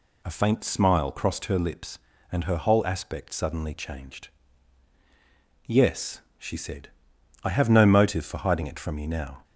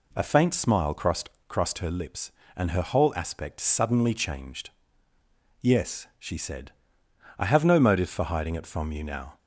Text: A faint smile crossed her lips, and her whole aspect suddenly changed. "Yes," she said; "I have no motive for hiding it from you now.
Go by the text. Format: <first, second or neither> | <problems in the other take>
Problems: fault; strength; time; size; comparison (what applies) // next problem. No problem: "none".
first | says "crossed" twice; at 1.4 s